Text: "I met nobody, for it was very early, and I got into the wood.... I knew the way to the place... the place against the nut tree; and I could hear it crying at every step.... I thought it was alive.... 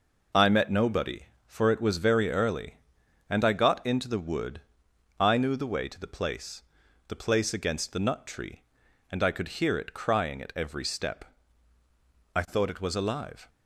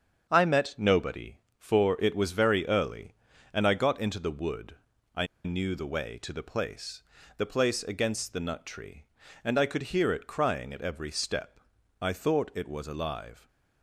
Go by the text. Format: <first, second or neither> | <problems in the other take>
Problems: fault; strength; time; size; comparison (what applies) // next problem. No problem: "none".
first | starts louder than the rest; strong; until 1.3 s; 7.5 dB // pauses between "I" and "knew"; slight; at 5.2 s; 0.19 s long